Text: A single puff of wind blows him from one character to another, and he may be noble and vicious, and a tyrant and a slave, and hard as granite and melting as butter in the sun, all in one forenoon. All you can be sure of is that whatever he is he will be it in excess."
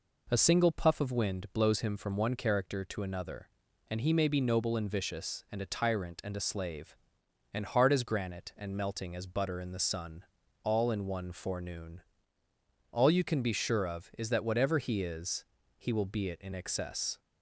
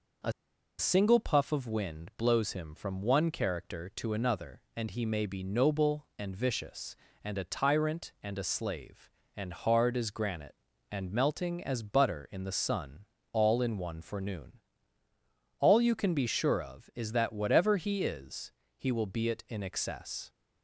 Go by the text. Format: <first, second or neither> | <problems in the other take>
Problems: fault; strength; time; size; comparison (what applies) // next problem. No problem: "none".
first | pauses between "A" and "single"; noticeable; at 0.3 s; 0.48 s long // pauses between "is" and "he"; slight; at 18.5 s; 0.26 s long; slight in the first